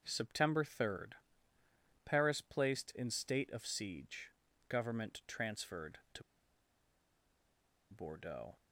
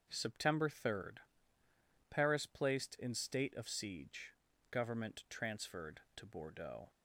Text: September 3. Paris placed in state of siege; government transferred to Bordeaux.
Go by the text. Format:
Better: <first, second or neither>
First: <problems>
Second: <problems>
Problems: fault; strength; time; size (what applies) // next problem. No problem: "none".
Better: second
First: starts louder than the rest; until 1.0 s; 6.5 dB // pauses between "to" and "Bordeaux"; strong; at 6.2 s; 1.6 s long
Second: starts louder than the rest; until 1.1 s; 6.5 dB